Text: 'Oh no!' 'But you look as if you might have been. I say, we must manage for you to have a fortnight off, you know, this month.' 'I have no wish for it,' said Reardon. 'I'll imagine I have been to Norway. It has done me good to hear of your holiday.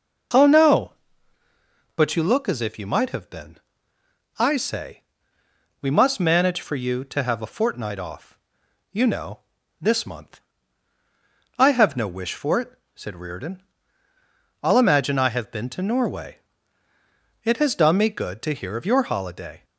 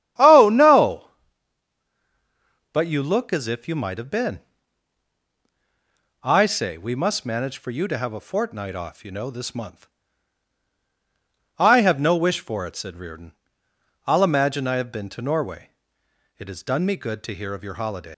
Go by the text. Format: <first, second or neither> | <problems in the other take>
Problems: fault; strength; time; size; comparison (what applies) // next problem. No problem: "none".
first | starts louder than the rest; strong; until 2.8 s; 11 dB // leaves "holiday" unfinished; at 18.1 s; 110 ms